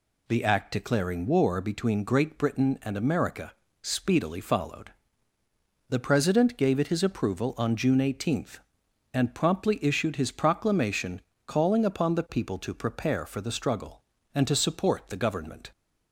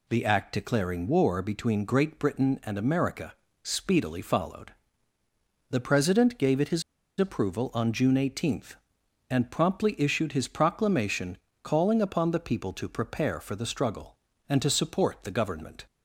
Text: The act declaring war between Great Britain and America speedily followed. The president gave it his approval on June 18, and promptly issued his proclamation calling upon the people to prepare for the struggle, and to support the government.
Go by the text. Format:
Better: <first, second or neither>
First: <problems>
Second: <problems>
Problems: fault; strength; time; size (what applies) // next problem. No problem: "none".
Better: first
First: pauses between "America" and "speedily"; slight; at 3.5 s; 0.30 s long // pauses between "proclamation" and "calling"; slight; at 11.2 s; 0.26 s long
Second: pauses between "America" and "speedily"; slight; at 3.3 s; 0.30 s long // pauses between "his" and "approval"; at 6.8 s; 0.38 s long // pauses between "proclamation" and "calling"; slight; at 11.3 s; 0.26 s long